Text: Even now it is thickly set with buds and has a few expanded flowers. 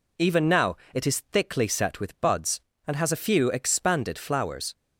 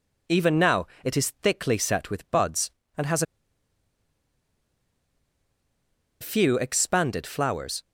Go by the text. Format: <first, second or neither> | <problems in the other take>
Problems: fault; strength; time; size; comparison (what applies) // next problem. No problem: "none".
first | pauses between "now" and "it"; slight; at 0.8 s; 0.18 s long; slight in the first // pauses between "has" and "a"; strong; at 3.2 s; 2.9 s long